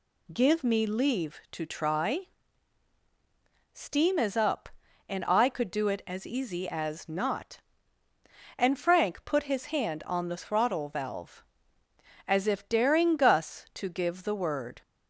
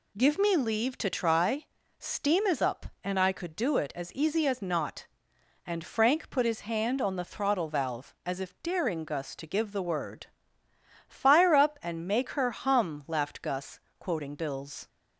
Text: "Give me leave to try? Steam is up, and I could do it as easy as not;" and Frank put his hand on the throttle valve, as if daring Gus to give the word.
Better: first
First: none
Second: goes on to say "Fire up and make her hum laughed Gus quoting Bill's"; strong; from 11.0 s on; 3.8 s long

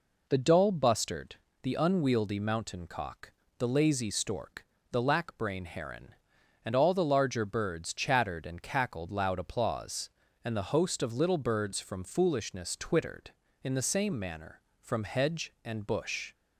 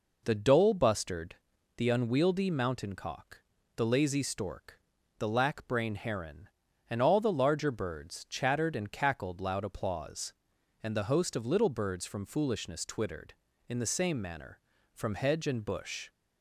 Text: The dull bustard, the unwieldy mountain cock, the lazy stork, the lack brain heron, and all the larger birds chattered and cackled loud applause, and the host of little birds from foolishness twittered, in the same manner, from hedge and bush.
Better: neither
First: none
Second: none

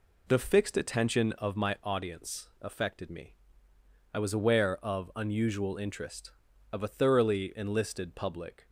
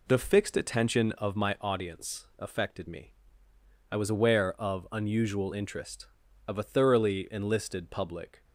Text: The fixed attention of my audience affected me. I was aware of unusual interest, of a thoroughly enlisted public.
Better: neither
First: none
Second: none

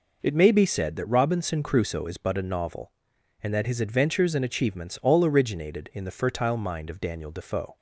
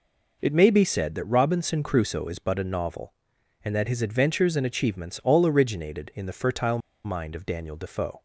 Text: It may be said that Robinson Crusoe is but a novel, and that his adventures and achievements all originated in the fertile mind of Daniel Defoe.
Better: first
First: none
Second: pauses between "fertile" and "mind"; slight; at 6.7 s; 0.26 s long

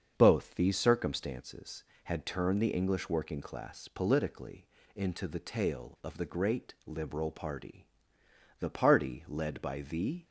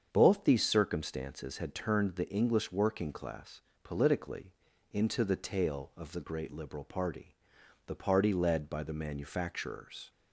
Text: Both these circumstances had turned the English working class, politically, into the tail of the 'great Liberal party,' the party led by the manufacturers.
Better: second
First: starts louder than the rest; until 1.1 s; 7 dB // stops before "manufacturers"; at 10.2 s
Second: starts louder than the rest; strong; until 1.1 s; 7.5 dB

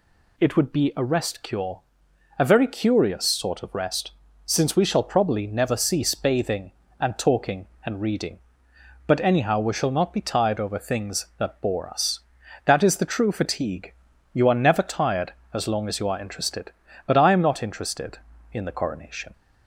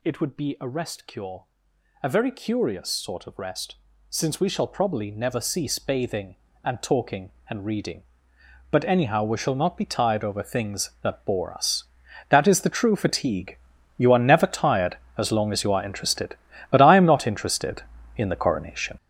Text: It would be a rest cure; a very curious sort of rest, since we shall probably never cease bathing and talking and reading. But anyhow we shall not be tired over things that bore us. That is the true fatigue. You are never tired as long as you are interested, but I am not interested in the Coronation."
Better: first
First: none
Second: gets louder; strong; throughout; 9.5 dB

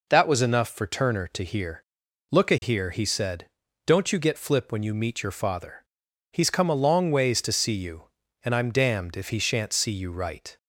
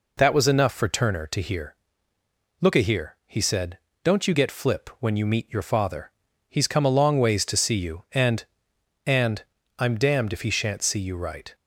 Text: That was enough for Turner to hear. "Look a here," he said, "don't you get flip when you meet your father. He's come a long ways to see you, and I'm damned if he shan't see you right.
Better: first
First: none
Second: says "and" twice; at 9.0 s

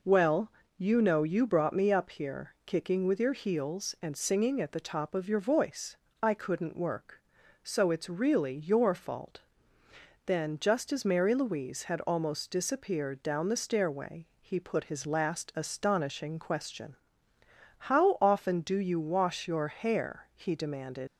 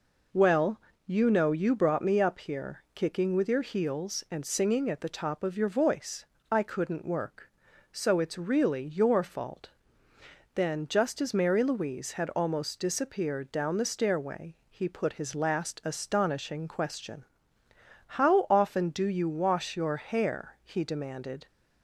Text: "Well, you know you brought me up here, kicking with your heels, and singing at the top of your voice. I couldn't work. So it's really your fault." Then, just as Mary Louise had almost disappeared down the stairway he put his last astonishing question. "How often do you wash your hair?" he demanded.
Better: second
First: leaves "demanded" unfinished; at 21.0 s; 105 ms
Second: none

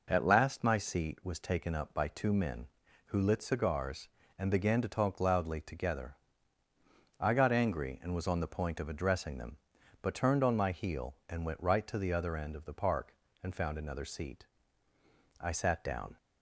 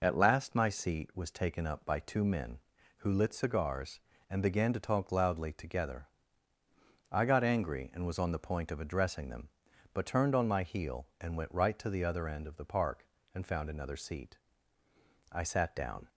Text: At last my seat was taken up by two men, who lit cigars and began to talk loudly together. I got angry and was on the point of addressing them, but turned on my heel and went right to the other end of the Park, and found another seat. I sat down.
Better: first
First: none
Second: loses the start of "At"; at 0.0 s; 30 ms

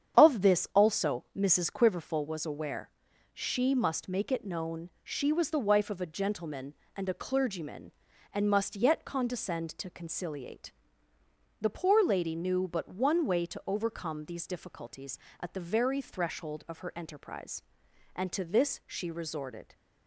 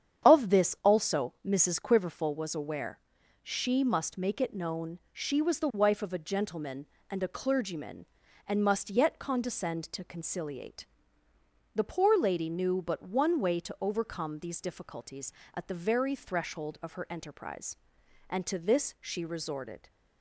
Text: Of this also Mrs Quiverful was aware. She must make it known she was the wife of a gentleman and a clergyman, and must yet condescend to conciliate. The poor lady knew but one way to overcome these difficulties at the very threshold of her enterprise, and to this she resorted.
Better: neither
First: starts louder than the rest; strong; until 1.2 s; 8.5 dB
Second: starts louder than the rest; strong; until 1.3 s; 8.5 dB

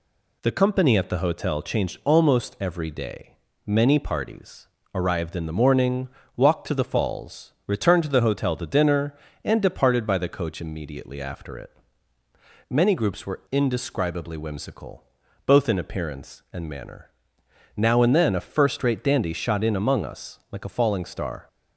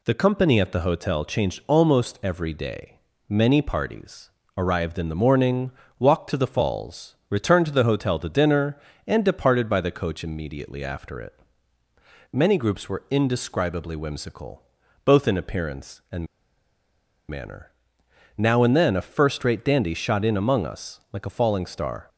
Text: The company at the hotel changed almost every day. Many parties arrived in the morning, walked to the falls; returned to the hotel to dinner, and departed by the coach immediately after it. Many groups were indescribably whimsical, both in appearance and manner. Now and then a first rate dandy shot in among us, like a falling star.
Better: first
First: pauses between "parties" and "arrived"; slight; at 4.6 s; 0.26 s long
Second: pauses between "parties" and "arrived"; slight; at 4.3 s; 0.26 s long // pauses between "and" and "manner"; at 16.2 s; 1.0 s long

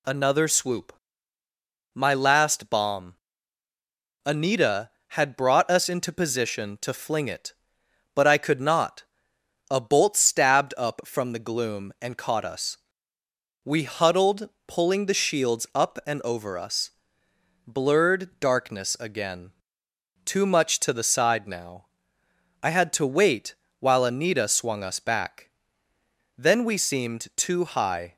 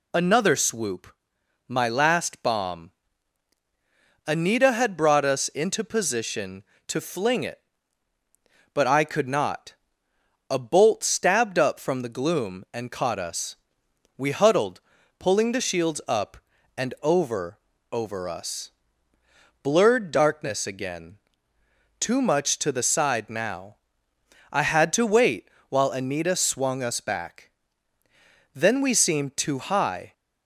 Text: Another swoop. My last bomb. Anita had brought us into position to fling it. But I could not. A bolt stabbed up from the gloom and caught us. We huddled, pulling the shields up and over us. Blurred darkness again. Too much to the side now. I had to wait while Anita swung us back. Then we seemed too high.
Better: first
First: pauses between "wait" and "while"; slight; at 23.5 s; 0.24 s long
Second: says "over" twice; at 17.9 s // pauses between "wait" and "while"; slight; at 25.4 s; 0.20 s long

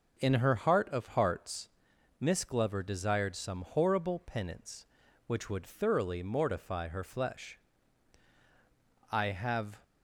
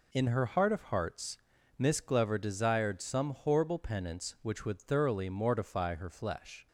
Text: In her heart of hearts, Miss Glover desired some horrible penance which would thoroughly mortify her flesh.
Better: second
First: goes on to say "I have"; noticeable; from 9.1 s on; 0.66 s long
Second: none

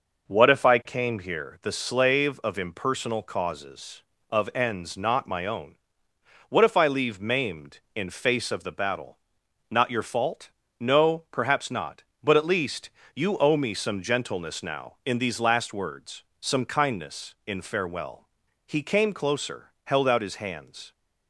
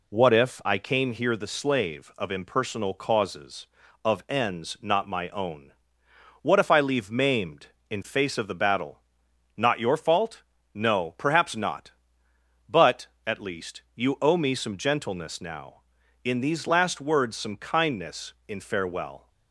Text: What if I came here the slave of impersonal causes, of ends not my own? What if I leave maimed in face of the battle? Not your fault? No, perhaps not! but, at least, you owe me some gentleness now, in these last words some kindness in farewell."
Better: second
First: pauses between "words" and "some"; slight; at 16.2 s; 0.18 s long // goes on to say "He came closer held out his hands"; strong; from 18.6 s on; 2.2 s long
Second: none

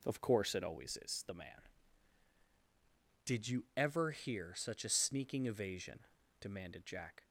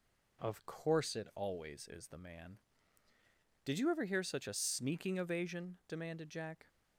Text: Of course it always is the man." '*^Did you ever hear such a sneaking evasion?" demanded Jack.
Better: neither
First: none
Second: none

